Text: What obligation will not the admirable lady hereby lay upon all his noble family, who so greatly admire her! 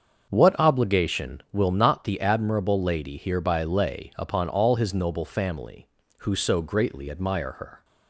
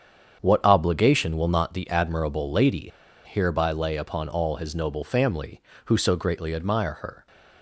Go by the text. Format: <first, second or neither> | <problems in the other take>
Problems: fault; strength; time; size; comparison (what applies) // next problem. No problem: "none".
first | starts louder than the rest; strong; until 1.4 s; 7.5 dB; also in the first // pauses between "lady" and "hereby"; at 2.9 s; 0.38 s long